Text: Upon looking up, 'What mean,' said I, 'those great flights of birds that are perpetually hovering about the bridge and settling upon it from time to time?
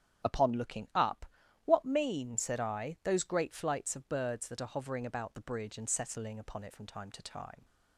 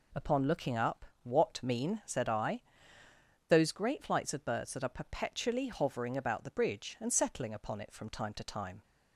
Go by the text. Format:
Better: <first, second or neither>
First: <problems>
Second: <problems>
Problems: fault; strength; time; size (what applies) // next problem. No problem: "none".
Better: second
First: starts louder than the rest; strong; until 1.7 s; 10 dB // skips "perpetually"; at 4.6 s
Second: none